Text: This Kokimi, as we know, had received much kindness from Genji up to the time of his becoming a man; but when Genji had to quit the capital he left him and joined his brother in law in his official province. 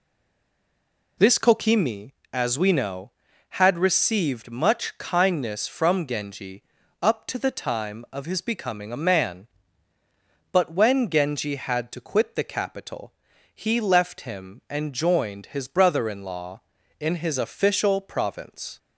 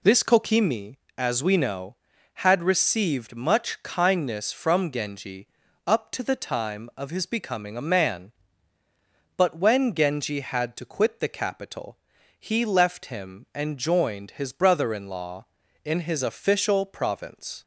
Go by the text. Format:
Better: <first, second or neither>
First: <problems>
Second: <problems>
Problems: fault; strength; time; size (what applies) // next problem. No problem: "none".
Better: second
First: stays silent before the first word; noticeable; until 1.1 s; 1.1 s long // pauses between "Genji" and "up"; at 6.6 s; 0.40 s long // pauses between "capital" and "he"; at 13.1 s; 0.40 s long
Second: pauses between "Genji" and "up"; at 5.4 s; 0.40 s long // pauses between "capital" and "he"; at 11.9 s; 0.40 s long